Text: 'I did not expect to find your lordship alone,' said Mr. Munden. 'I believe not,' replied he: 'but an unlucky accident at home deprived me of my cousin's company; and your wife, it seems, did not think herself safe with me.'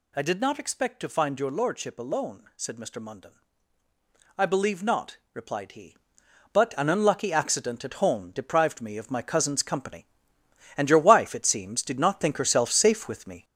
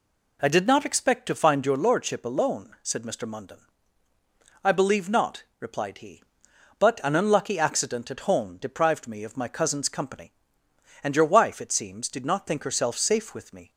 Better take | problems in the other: second | gets louder; noticeable; throughout; 5 dB

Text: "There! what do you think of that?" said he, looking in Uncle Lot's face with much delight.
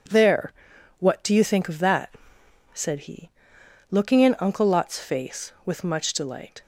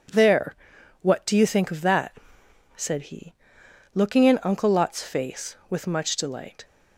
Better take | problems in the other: neither | none

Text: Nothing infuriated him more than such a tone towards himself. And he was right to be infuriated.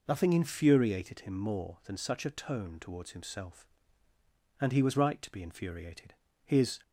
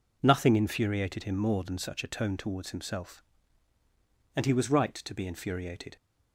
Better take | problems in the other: second | goes on to say "His"; slight; from 6.4 s on; 0.36 s long

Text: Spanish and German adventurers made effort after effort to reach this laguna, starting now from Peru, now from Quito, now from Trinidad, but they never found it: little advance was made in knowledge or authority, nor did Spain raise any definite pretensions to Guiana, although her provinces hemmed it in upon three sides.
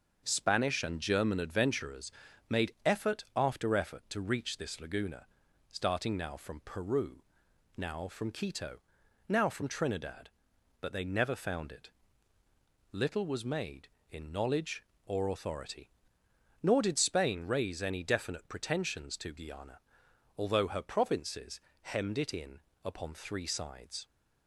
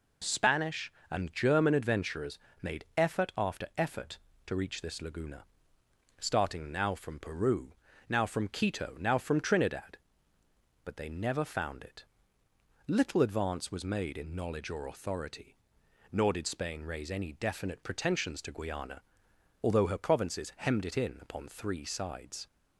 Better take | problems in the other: second | starts louder than the rest; until 1.2 s; 6.5 dB // pauses between "adventurers" and "made"; at 2.0 s; 0.38 s long; slight in the second // skips "advance"; at 13.2 s // pauses between "provinces" and "hemmed"; slight; at 21.5 s; 0.22 s long // pauses between "in" and "upon"; slight; at 22.5 s; 0.22 s long

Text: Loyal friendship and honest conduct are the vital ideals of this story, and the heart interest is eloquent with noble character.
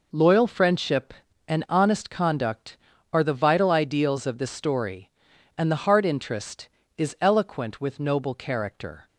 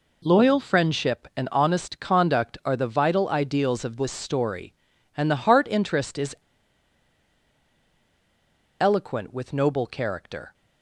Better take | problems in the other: first | pauses between "is" and "eloquent"; strong; at 6.3 s; 2.4 s long

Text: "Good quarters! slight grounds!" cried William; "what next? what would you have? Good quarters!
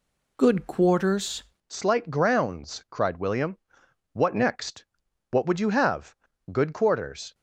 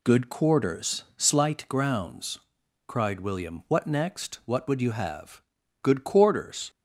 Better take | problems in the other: second | changes voice at "slight"; from 1.7 s on; 5.6 s long

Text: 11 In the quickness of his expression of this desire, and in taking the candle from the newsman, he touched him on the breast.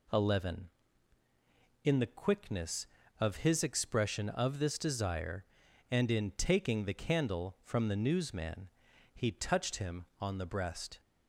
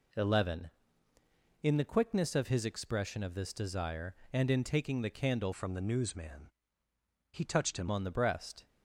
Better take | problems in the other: first | changes voice from "from" to "him"; from 5.5 to 7.8 s; 2.3 s long

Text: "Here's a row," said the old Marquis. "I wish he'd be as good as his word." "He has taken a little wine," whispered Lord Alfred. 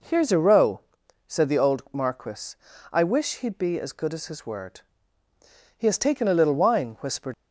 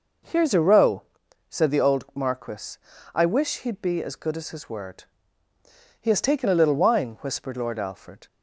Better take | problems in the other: second | stops before "Lord Alfred"; at 7.3 s

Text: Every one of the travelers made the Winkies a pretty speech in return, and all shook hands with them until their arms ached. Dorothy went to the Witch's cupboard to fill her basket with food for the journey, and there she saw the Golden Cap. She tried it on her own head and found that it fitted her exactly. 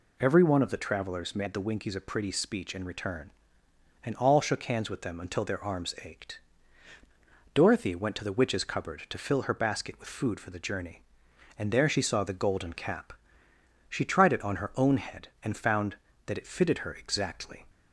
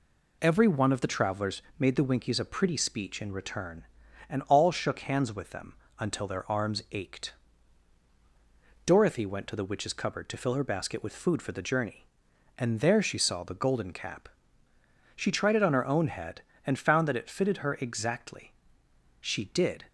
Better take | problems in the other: first | pauses between "travelers" and "made"; slight; at 1.6 s; 0.18 s long // pauses between "them" and "until"; slight; at 5.7 s; 0.24 s long // goes on to say "She did"; noticeable; from 19.2 s on; 0.64 s long

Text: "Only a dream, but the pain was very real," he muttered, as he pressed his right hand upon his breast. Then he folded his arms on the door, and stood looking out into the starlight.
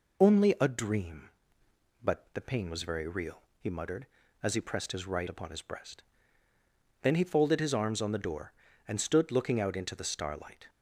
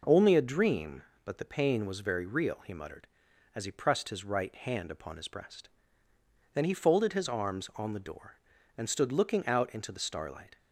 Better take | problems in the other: second | skips "hand"; at 5.2 s

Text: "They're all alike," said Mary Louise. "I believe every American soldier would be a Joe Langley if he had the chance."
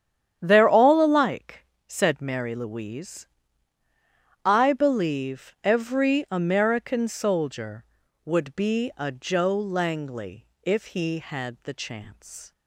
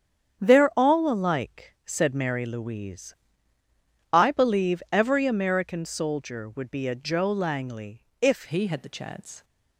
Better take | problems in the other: first | starts louder than the rest; strong; until 1.4 s; 8.5 dB; strong in the first // pauses between "Langley" and "if"; slight; at 8.0 s; 0.16 s long // changes voice at "he"; from 8.4 s on; 1.0 s long

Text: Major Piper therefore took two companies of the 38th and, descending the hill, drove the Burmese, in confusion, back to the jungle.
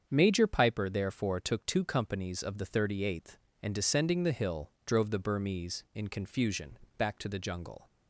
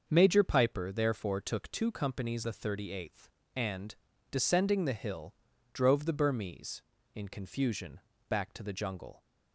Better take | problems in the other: first | starts louder than the rest; until 1.0 s; 6.5 dB; strong in the first // skips "of"; at 2.4 s

